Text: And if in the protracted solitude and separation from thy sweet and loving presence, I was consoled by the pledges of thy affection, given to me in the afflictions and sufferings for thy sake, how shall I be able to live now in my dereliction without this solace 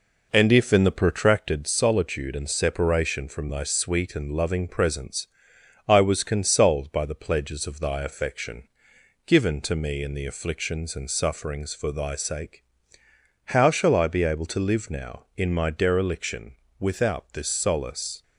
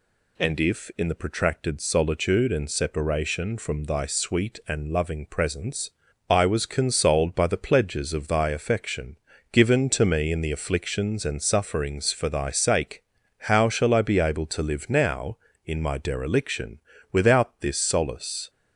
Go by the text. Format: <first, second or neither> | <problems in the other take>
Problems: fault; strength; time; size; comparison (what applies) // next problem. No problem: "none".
second | starts louder than the rest; noticeable; until 1.7 s; 4.5 dB // pauses between "dereliction" and "without"; slight; at 16.5 s; 0.26 s long; slight in the second